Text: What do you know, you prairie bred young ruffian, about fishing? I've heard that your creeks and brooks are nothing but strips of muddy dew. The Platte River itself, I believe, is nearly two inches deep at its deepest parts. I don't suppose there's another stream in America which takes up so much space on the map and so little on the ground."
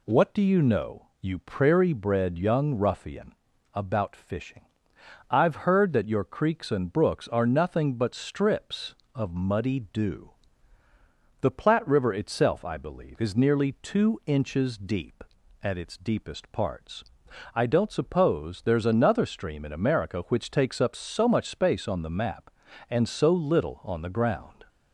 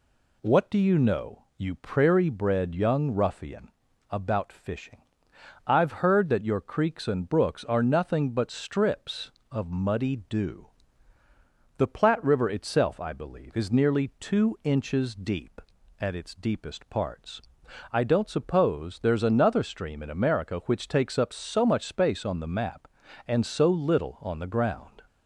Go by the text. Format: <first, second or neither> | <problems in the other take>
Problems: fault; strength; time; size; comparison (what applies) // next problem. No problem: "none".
neither | none